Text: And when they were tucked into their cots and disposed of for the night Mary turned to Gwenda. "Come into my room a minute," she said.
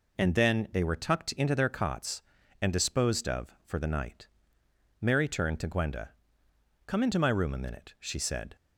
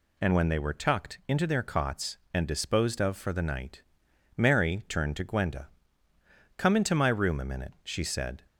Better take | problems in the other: second | says "then" for "when"; at 0.3 s // pauses between "night" and "Mary"; noticeable; at 4.2 s; 0.74 s long; noticeable in the second

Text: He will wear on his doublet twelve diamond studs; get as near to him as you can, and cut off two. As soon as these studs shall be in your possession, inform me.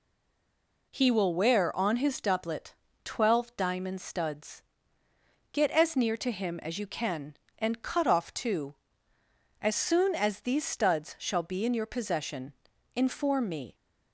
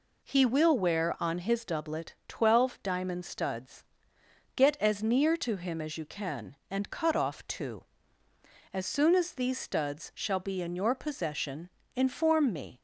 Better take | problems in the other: second | stays silent before the first word; slight; until 0.9 s; 0.9 s long // pauses between "doublet" and "twelve"; slight; at 2.7 s; 0.32 s long

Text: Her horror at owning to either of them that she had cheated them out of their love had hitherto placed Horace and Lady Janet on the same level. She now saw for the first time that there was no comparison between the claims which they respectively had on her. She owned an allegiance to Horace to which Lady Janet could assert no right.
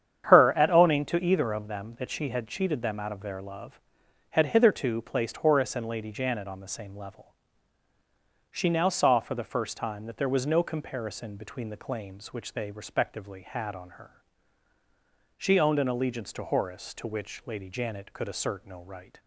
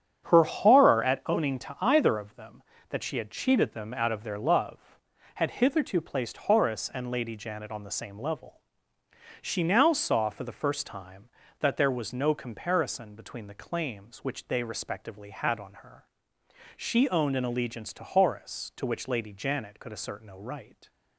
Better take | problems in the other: second | starts louder than the rest; strong; until 1.2 s; 8.5 dB; strong in the second // skips "horror"; at 0.5 s

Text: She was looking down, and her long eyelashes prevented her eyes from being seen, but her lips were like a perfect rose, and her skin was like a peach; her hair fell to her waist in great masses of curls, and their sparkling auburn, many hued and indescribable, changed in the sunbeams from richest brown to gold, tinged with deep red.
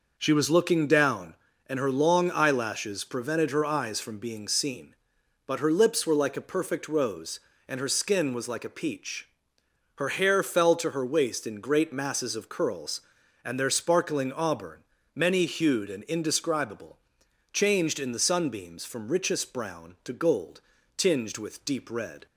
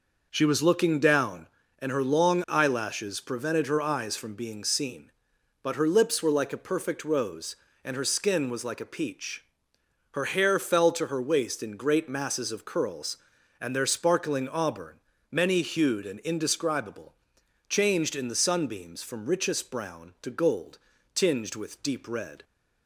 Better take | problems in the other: neither | none

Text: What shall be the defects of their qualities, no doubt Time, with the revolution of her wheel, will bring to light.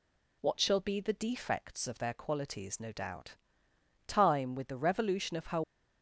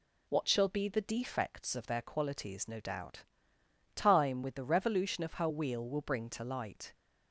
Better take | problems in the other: second | pauses between "doubt" and "Time"; noticeable; at 3.3 s; 0.72 s long; noticeable in the second // stops before "wheel will bring to light"; at 5.6 s

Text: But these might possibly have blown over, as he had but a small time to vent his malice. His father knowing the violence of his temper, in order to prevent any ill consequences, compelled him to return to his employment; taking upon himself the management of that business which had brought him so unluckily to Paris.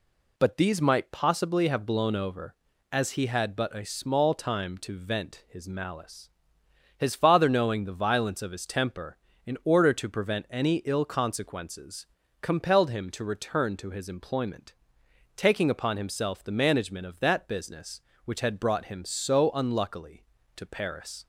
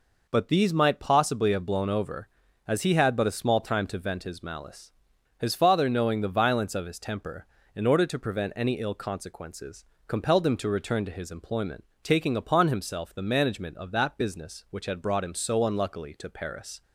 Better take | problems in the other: neither | none

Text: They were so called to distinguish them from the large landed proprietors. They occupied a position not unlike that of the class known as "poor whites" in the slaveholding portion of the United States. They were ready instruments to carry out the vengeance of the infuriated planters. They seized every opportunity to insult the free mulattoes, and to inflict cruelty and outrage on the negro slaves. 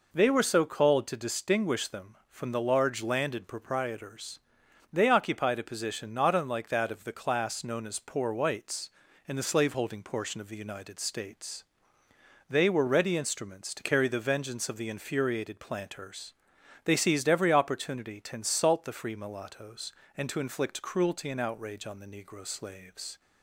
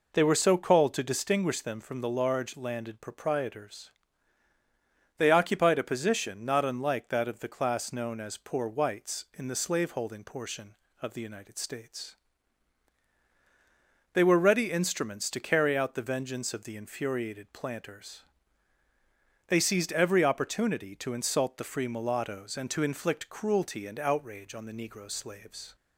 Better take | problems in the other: second | skips "out"; at 14.0 s

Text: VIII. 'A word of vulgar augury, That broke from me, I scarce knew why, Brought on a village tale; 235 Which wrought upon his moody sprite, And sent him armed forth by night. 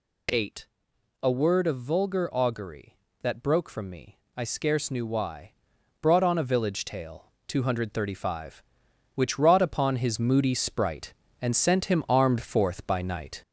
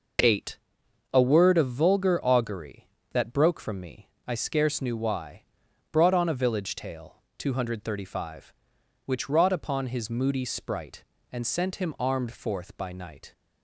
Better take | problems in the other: second | gets louder; noticeable; throughout; 4.5 dB

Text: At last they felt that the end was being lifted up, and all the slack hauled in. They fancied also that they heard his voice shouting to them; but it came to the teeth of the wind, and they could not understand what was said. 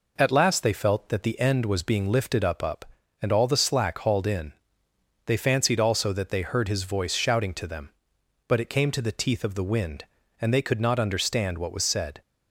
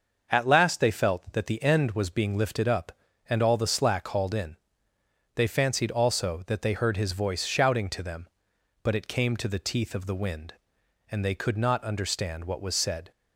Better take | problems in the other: second | says "up" twice; at 2.6 s

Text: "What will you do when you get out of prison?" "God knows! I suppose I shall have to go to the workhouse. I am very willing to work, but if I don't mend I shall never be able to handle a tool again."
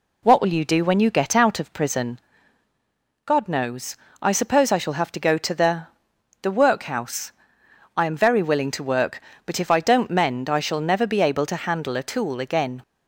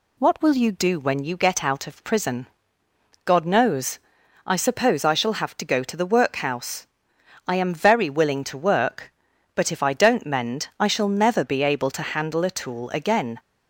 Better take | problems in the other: second | says "the" twice; at 6.3 s

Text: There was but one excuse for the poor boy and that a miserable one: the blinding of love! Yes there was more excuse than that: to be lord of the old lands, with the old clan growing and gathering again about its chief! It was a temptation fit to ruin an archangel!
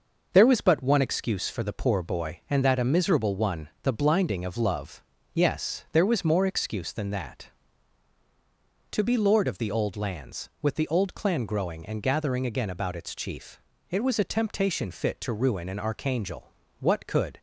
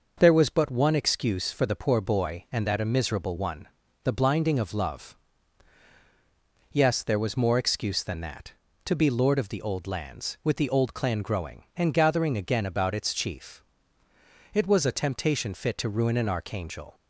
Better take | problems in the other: second | goes on to say "What could"; from 16.7 s on; 0.60 s long

